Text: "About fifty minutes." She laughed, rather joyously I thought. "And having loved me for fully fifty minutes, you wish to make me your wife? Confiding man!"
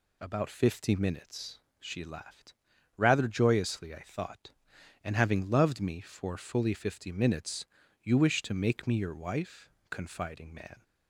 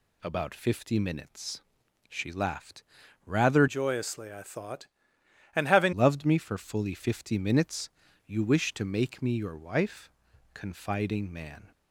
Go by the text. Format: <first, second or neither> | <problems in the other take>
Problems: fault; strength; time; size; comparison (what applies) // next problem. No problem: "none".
first | changes voice from "joyously" to "having"; from 3.6 to 5.9 s; 2.3 s long